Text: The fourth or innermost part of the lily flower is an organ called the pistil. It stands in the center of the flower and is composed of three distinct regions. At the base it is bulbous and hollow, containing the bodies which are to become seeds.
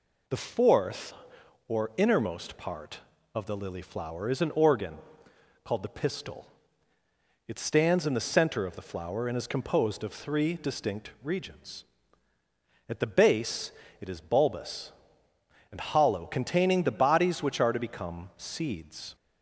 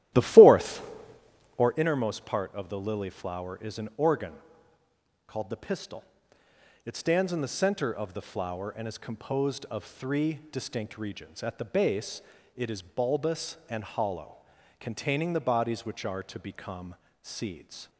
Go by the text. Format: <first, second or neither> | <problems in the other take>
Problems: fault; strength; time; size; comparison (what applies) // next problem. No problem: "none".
first | starts louder than the rest; strong; until 1.9 s; 14 dB // pauses between "organ" and "called"; noticeable; at 4.3 s; 0.94 s long; noticeable in the first // pauses between "base" and "it"; slight; at 12.2 s; 0.36 s long; slight in the first // pauses between "become" and "seeds"; slight; at 16.9 s; 0.26 s long